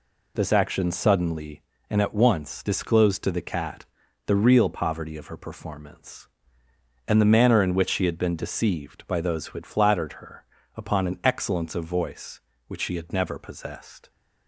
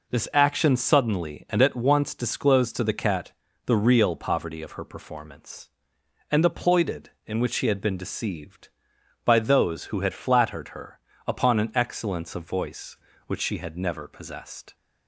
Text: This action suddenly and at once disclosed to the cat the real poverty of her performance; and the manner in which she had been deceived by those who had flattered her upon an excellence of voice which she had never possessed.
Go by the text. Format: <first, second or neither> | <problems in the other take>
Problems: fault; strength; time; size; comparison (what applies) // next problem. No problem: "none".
first | pauses between "cat" and "the"; slight; at 3.3 s; 0.32 s long; also in the first // says "ploited" for "manner"; at 6.4 s // pauses between "her" and "upon"; slight; at 10.9 s; 0.28 s long; slight in the first